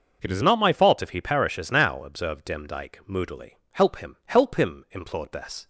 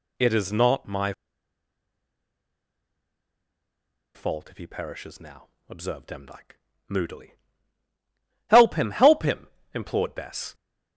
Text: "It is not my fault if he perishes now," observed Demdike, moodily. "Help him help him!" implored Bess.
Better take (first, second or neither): first